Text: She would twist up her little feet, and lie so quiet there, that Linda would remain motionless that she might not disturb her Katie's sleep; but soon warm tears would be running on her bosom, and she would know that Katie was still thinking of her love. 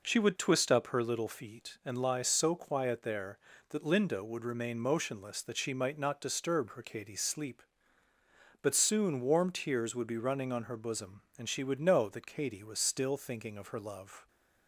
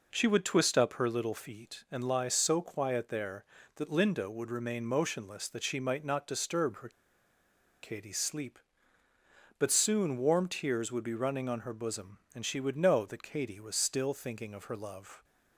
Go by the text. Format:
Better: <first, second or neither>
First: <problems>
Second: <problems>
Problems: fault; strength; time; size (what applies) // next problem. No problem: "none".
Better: first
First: none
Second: pauses between "her" and "Katie's"; noticeable; at 6.8 s; 0.93 s long